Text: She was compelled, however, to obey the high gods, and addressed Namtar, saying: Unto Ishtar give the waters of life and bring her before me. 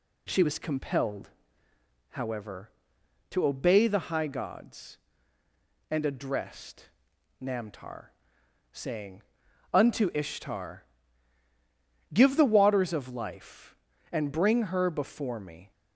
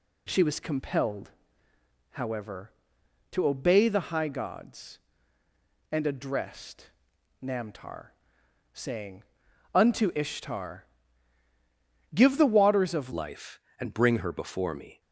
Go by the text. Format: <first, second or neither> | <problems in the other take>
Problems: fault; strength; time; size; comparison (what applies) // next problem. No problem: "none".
first | pauses between "addressed" and "Namtar"; noticeable; at 6.8 s; 0.52 s long; noticeable in the first // pauses between "Ishtar" and "give"; strong; at 10.8 s; 1.3 s long; strong in the first // changes voice at "life"; from 13.1 s on; 1.9 s long